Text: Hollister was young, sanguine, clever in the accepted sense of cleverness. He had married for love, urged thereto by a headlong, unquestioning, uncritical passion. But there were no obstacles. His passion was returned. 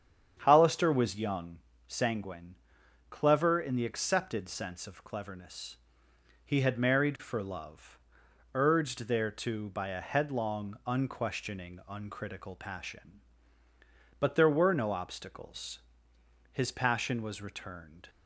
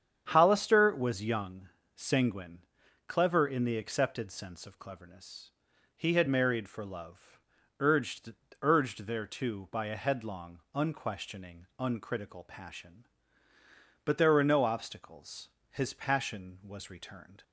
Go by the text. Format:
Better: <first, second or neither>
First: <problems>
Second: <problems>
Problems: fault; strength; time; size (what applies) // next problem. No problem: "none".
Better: first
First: starts louder than the rest; strong; until 1.4 s; 8 dB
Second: starts louder than the rest; strong; until 1.3 s; 8 dB // says "urged" twice; at 8.6 s